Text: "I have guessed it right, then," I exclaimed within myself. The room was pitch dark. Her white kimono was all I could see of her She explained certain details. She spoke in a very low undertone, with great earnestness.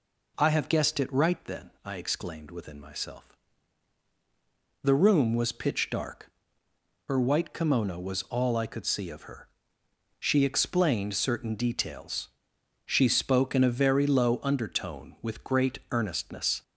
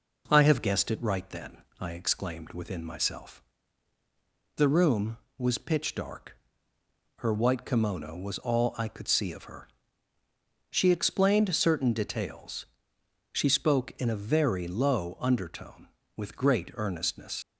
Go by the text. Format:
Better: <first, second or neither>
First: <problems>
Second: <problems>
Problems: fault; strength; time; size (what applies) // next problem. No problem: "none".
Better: first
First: pauses between "her" and "She"; noticeable; at 9.4 s; 0.72 s long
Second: pauses between "her" and "She"; at 9.6 s; 1.0 s long // leaves "earnestness" unfinished; at 17.4 s; 60 ms